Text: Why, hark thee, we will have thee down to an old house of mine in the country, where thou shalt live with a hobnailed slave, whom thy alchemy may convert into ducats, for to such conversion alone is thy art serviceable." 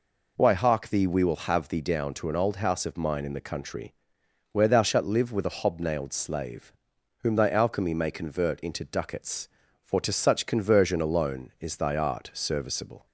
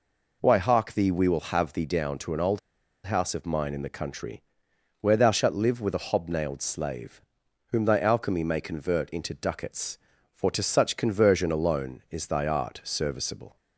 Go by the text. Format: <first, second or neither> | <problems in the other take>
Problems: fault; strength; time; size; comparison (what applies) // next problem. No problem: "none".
first | pauses between "old" and "house"; noticeable; at 2.5 s; 0.46 s long